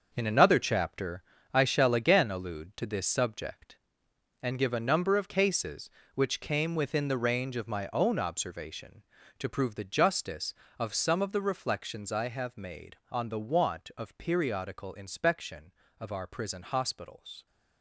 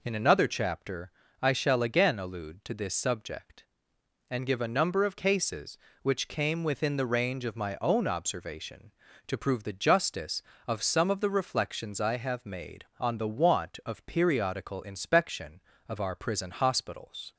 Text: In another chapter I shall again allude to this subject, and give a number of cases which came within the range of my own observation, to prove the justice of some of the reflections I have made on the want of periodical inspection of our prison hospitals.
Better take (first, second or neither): second